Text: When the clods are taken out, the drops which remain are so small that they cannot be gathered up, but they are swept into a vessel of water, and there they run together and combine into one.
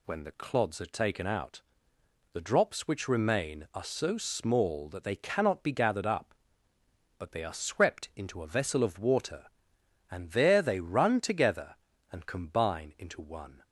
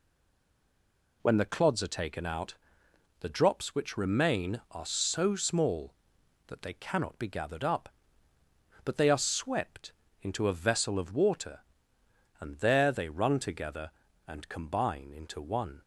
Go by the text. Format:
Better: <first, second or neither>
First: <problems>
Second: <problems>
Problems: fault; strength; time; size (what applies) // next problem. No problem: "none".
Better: first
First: none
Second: stays silent before the first word; noticeable; until 1.2 s; 1.2 s long // pauses between "swept" and "into"; slight; at 9.9 s; 0.30 s long